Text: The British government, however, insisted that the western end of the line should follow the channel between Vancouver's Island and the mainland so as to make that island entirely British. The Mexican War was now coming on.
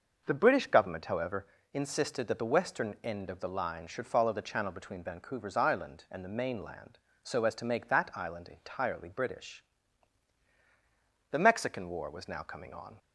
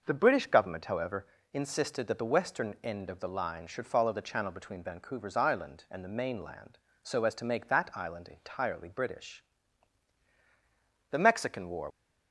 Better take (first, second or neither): first